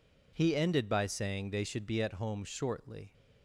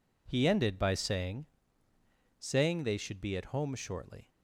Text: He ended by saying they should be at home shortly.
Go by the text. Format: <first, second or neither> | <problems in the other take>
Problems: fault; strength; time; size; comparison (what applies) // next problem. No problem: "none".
first | says "saying" twice; at 2.3 s